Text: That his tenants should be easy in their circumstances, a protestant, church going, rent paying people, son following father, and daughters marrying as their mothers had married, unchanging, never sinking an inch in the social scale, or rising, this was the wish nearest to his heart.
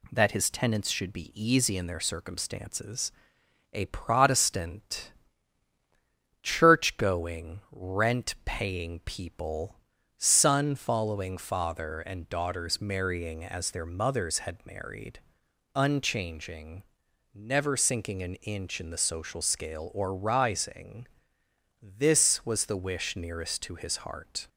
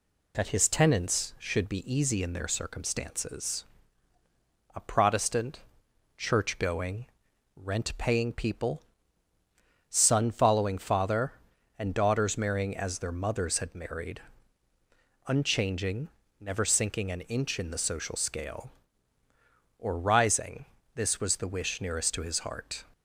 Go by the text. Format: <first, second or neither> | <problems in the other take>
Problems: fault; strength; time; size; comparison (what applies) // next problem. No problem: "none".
neither | none